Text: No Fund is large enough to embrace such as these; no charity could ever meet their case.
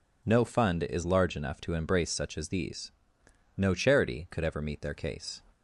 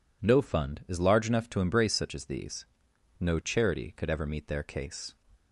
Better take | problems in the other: neither | none

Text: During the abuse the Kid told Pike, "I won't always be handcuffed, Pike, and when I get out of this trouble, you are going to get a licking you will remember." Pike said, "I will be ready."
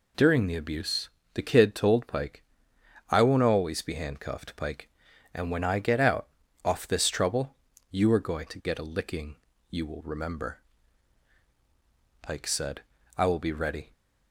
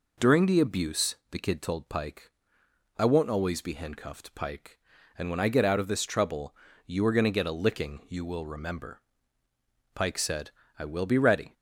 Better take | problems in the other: second | pauses between "abuse" and "the"; slight; at 1.0 s; 0.24 s long; slight in the second // says "off" for "of"; at 6.6 s // pauses between "licking" and "you"; slight; at 9.3 s; 0.34 s long

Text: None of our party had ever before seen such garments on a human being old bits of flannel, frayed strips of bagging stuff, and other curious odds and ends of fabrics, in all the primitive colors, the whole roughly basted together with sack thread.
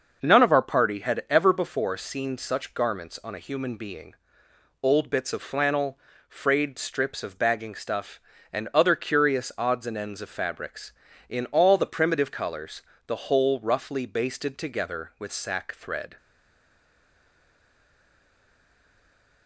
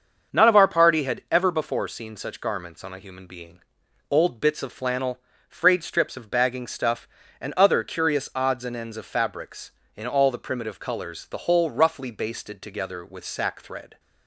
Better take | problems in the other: second | starts louder than the rest; noticeable; until 1.2 s; 6 dB; also in the second // pauses between "being" and "old"; noticeable; at 4.1 s; 0.66 s long; noticeable in the second // stays silent after the last word; strong; from 16.1 s on; 3.3 s long

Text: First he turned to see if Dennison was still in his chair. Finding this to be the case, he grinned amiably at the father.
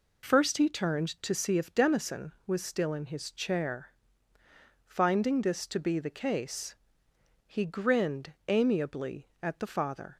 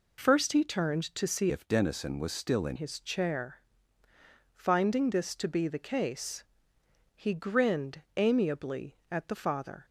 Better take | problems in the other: first | changes voice from "if" to "in"; from 1.5 to 2.7 s; 1.2 s long // pauses between "grinned" and "amiably"; slight; at 8.0 s; 0.16 s long; slight in the first

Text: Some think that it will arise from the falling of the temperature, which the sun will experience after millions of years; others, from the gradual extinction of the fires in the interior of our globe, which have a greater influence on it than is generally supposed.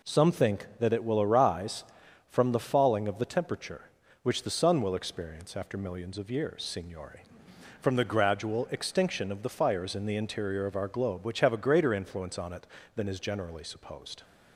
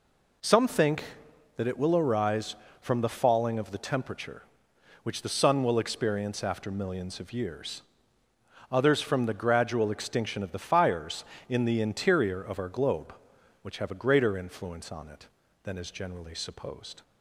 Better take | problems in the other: second | says "signore" for "others"; at 6.6 s

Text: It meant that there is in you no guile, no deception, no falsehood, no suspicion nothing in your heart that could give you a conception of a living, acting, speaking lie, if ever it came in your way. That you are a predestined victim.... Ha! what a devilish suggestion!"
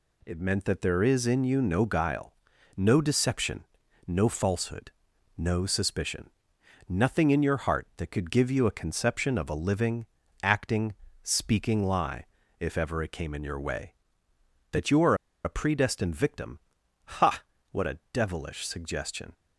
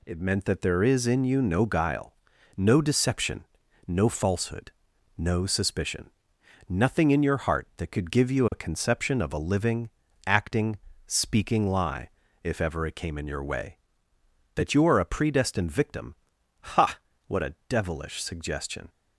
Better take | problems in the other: second | pauses between "suspicion" and "nothing"; noticeable; at 6.2 s; 0.62 s long; noticeable in the second // pauses between "are" and "a"; slight; at 15.1 s; 0.29 s long // pauses between "a" and "devilish"; slight; at 17.9 s; 0.16 s long; slight in the second

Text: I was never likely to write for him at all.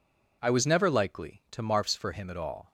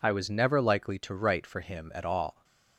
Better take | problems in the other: second | says "marfs" for "write"; at 1.6 s

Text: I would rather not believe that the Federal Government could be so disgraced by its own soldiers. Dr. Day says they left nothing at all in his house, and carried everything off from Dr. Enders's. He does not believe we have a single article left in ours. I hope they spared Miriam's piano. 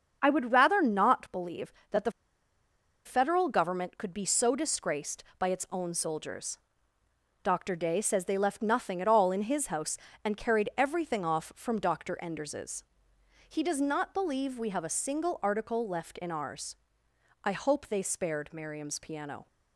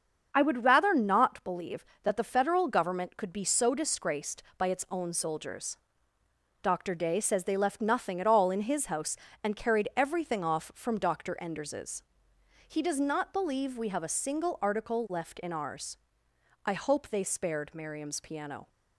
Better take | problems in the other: second | starts louder than the rest; until 1.2 s; 7 dB; also in the second // pauses between "the" and "Federal"; noticeable; at 2.1 s; 0.93 s long

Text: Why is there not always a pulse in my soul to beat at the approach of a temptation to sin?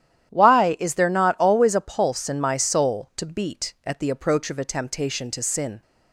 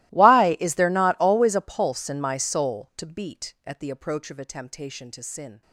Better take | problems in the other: first | gets quieter; strong; throughout; 27 dB // starts louder than the rest; strong; until 1.1 s; 19 dB; strong in the first

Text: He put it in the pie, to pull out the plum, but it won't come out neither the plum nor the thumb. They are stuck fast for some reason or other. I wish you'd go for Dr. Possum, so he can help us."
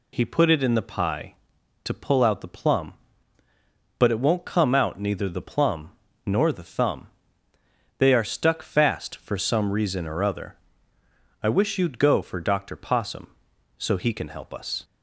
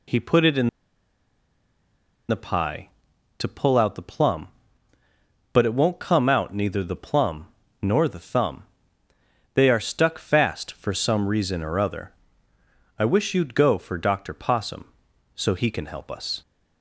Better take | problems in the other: first | pauses between "in" and "the"; strong; at 0.6 s; 1.6 s long // pauses between "plum" and "nor"; slight; at 7.4 s; 0.34 s long; slight in the first

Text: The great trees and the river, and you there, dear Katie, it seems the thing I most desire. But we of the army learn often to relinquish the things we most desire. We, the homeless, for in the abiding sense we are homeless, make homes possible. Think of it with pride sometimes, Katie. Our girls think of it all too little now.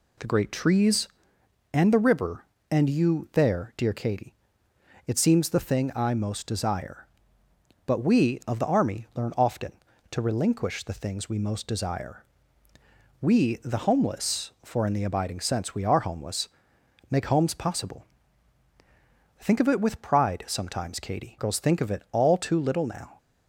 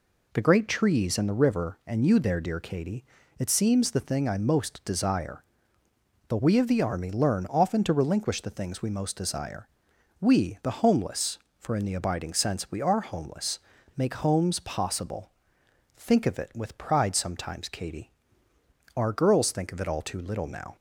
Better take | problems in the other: second | skips "Our"; at 21.3 s

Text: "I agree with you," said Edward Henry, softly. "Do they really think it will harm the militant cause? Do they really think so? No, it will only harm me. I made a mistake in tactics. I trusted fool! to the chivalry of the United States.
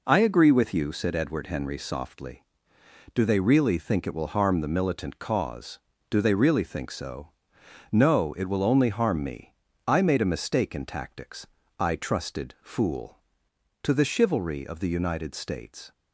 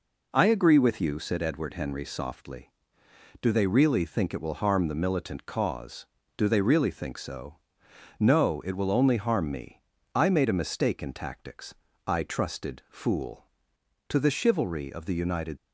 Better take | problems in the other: first | stops before "States"; at 15.5 s

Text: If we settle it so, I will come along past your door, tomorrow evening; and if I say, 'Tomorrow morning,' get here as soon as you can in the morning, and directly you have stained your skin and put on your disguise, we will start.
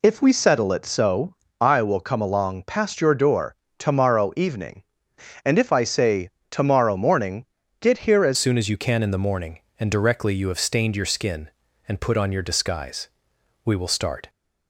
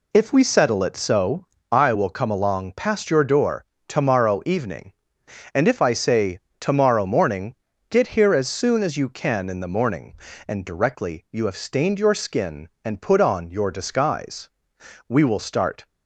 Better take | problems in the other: second | changes voice at "soon"; from 8.3 s on; 5.9 s long

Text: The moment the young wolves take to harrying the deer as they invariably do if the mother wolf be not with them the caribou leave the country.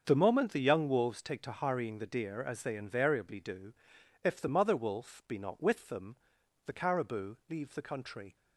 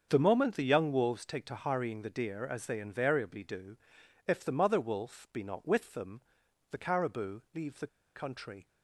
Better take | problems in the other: first | starts louder than the rest; until 1.1 s; 7 dB; also in the first // pauses between "do" and "if"; noticeable; at 3.7 s; 0.50 s long; noticeable in the first // pauses between "them" and "the"; noticeable; at 6.2 s; 0.48 s long; noticeable in the first // pauses between "the" and "country"; slight; at 7.8 s; 0.29 s long

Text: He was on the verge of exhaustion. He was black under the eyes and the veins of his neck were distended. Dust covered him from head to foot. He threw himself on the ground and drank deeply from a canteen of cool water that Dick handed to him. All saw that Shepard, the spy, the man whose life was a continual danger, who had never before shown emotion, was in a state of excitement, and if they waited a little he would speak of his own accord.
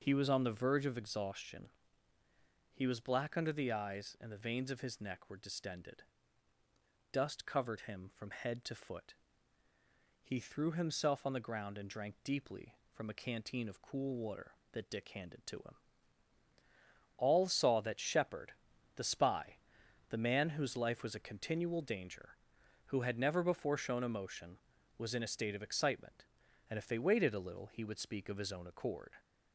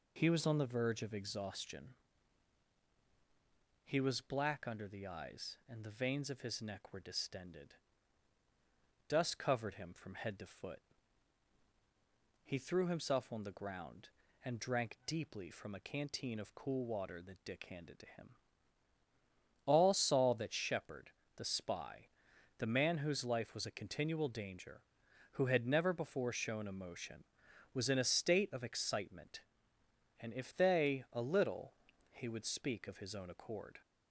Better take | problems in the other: first | skips "waited"; at 31.0 s // pauses between "little" and "he"; slight; at 31.7 s; 0.36 s long

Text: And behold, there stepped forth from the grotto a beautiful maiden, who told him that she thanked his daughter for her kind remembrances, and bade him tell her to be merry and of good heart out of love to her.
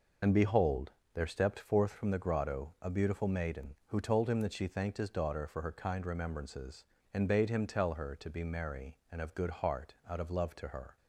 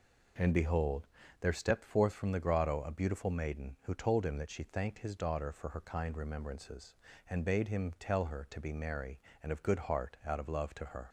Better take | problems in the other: second | loses the start of "And"; at 0.2 s; 70 ms

